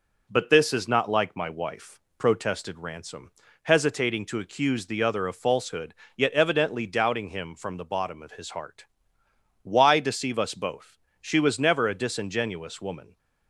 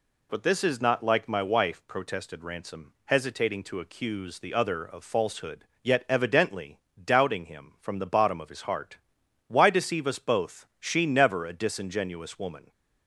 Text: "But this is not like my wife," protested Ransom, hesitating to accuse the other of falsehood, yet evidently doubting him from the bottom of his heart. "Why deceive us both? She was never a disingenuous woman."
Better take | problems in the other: first | pauses between "evidently" and "doubting"; slight; at 6.7 s; 0.24 s long // skips "was"; at 11.0 s

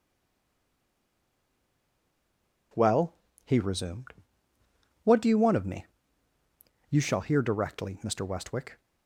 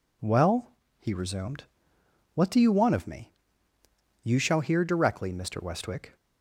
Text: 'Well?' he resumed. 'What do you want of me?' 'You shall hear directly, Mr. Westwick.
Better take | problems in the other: second | stays silent before the first word; strong; until 2.7 s; 2.7 s long

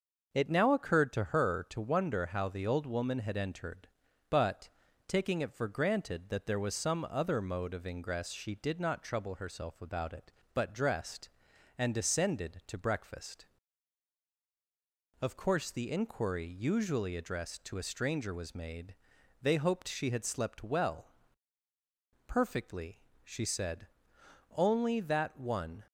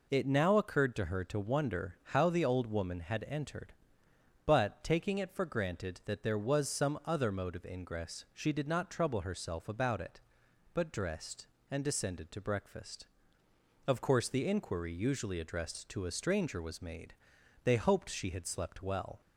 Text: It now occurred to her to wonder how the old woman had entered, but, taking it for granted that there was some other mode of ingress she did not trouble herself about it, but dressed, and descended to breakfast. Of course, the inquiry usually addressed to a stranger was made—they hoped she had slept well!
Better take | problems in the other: second | goes on to say "Perfectly she said only that one"; strong; from 22.2 s on; 3.6 s long

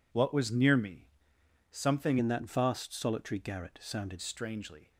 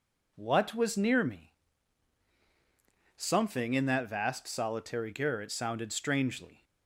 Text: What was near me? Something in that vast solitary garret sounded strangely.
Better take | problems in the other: second | changes voice from "in" to "sounded"; from 2.1 to 4.2 s; 2.1 s long

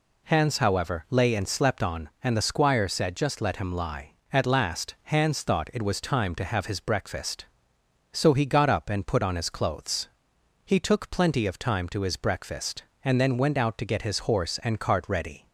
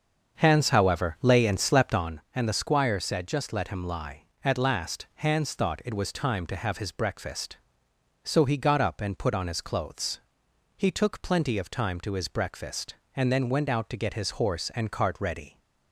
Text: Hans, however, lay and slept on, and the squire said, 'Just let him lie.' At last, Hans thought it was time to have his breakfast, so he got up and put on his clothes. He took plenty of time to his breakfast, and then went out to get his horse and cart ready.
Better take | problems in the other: first | starts louder than the rest; until 2.2 s; 7 dB

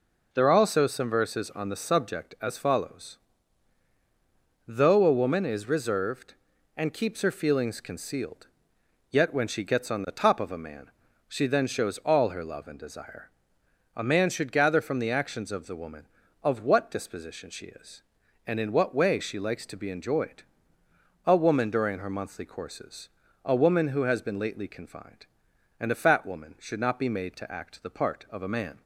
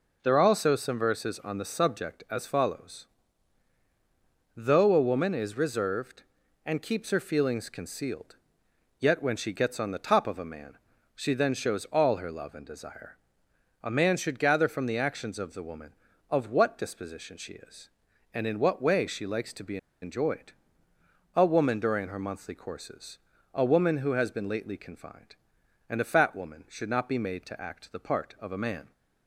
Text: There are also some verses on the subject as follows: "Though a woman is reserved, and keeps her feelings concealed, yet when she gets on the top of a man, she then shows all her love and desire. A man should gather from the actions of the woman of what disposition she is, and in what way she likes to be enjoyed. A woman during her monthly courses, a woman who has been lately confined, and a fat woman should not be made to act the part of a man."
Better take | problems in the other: first | pauses between "be" and "enjoyed"; slight; at 19.7 s; 0.24 s long

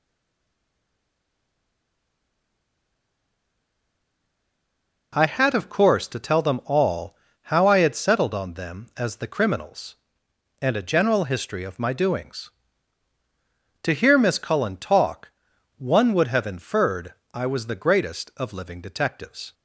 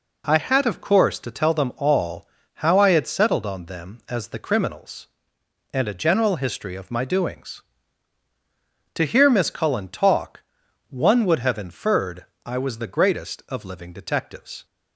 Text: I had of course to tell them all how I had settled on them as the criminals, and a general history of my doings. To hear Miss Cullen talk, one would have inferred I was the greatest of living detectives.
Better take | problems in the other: second | stays silent before the first word; strong; until 5.1 s; 5.1 s long // pauses between "all" and "how"; slight; at 7.1 s; 0.28 s long; slight in the second // pauses between "inferred" and "I"; slight; at 17.1 s; 0.18 s long; slight in the second

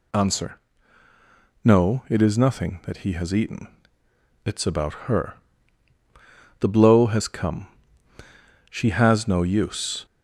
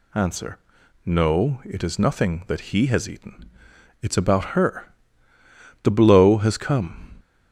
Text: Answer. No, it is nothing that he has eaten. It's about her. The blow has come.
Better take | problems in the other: second | goes on to say "She has no use"; from 8.7 s on; 1.3 s long

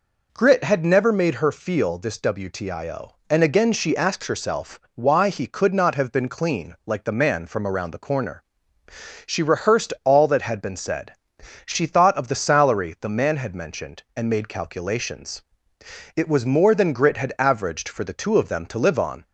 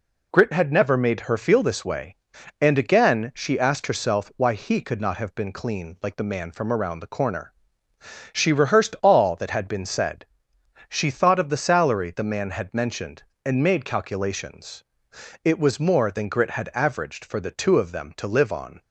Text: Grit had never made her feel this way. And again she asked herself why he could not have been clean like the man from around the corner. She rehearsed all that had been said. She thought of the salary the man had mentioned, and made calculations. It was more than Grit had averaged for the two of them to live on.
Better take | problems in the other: second | says "wtio" for "way"; at 2.1 s // pauses between "herself" and "why"; slight; at 4.7 s; 0.16 s long

